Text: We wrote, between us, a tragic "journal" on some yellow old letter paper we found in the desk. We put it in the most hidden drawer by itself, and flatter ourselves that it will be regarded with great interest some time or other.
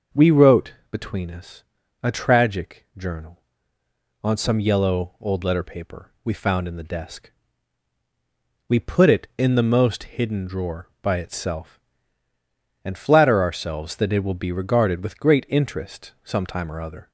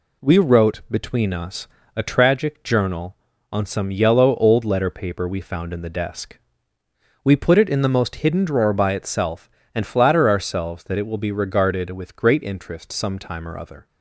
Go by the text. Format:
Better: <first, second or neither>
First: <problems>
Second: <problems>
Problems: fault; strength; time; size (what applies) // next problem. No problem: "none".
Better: neither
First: none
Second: none